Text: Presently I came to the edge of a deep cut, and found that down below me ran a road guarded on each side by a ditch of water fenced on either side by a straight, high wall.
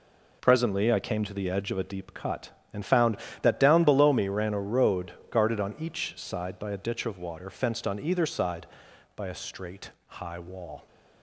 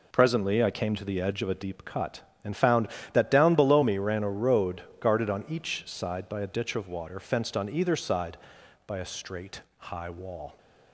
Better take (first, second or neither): neither